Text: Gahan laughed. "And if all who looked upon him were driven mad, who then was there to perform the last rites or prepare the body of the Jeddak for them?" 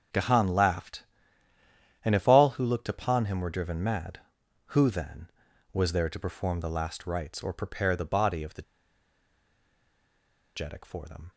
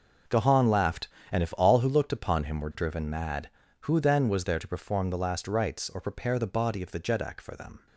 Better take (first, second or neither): second